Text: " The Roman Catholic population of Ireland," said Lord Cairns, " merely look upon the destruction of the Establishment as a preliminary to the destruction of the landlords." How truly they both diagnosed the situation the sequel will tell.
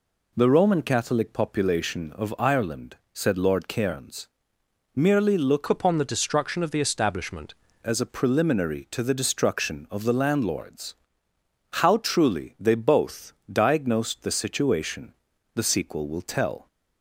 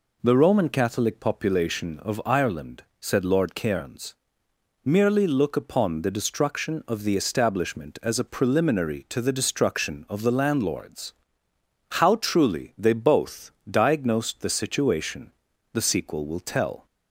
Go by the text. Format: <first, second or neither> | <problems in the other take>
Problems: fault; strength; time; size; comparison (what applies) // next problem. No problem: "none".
second | changes voice from "upon" to "Establishment"; from 5.6 to 7.5 s; 1.9 s long // pauses between "both" and "diagnosed"; slight; at 13.3 s; 0.18 s long; slight in the second // pauses between "situation" and "the"; at 15.1 s; 0.40 s long; also in the second